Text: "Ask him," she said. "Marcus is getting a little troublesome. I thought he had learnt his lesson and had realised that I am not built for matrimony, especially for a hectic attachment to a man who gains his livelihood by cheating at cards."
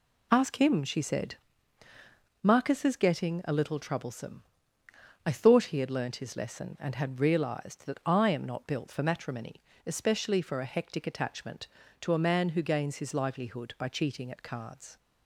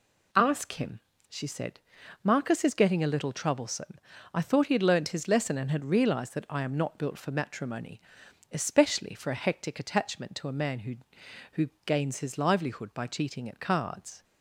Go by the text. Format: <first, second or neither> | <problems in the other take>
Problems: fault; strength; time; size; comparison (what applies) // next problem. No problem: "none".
first | says "who" twice; at 11.5 s